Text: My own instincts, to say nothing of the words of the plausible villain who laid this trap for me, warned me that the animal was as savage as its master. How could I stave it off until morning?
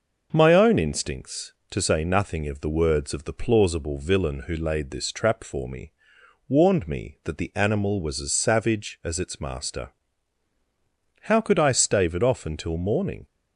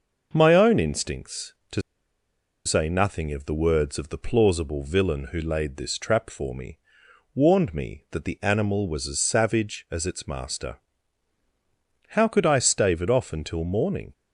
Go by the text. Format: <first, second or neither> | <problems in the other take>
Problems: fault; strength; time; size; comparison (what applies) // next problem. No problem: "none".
first | pauses between "to" and "say"; noticeable; at 1.8 s; 0.84 s long